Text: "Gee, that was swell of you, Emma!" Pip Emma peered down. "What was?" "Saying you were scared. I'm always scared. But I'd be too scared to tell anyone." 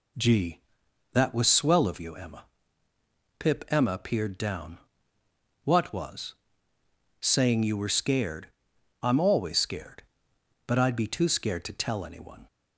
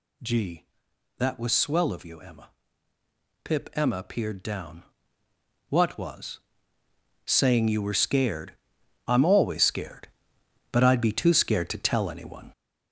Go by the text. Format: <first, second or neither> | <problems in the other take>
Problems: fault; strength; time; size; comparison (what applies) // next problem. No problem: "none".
first | gets louder; throughout; 6.5 dB